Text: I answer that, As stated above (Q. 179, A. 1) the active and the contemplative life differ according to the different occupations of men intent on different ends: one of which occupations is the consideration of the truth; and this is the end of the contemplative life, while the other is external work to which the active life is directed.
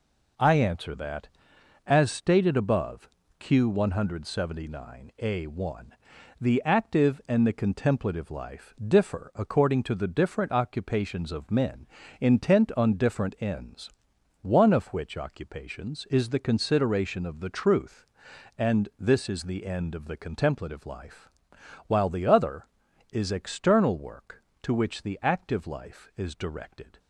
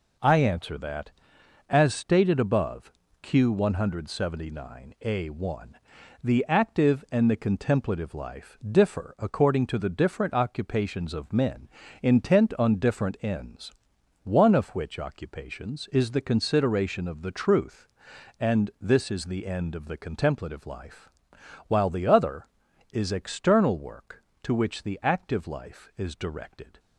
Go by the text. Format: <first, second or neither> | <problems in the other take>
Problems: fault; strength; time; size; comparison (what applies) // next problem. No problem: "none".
neither | pauses between "men" and "intent"; slight; the same in both